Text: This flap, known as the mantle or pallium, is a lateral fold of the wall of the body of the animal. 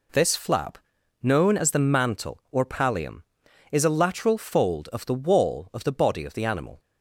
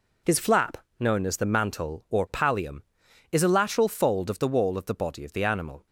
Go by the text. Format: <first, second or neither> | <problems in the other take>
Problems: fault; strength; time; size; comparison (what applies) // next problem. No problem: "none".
first | says "His" for "This"; at 0.2 s